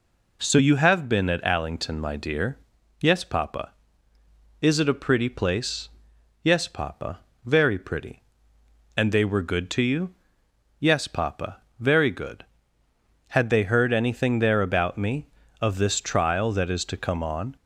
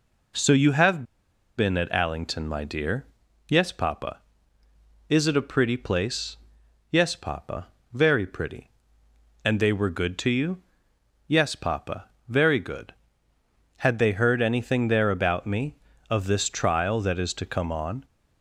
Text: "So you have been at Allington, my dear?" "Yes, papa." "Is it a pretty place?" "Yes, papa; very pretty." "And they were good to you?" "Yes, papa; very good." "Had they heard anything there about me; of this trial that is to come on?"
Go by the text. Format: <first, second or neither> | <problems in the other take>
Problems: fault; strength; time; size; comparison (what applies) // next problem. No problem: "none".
first | pauses between "have" and "been"; noticeable; at 1.0 s; 0.53 s long